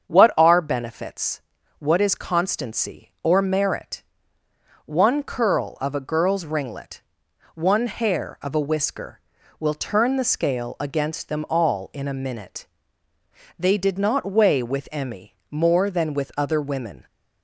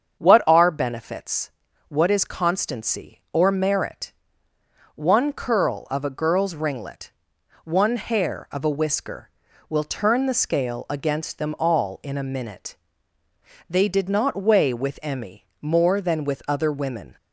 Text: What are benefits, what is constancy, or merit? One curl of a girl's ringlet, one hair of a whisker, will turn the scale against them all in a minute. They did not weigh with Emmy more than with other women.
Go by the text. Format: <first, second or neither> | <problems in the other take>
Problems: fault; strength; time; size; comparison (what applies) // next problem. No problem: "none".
neither | starts louder than the rest; strong; the same in both // pauses between "Emmy" and "more"; slight; the same in both